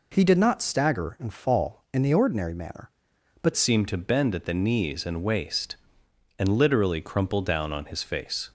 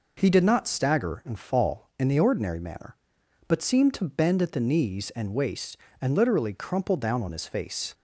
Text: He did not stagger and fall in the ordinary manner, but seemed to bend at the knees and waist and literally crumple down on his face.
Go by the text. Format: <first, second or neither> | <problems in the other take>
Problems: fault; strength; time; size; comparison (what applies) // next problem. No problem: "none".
second | changes voice at "seemed"; from 3.5 s on; 5.0 s long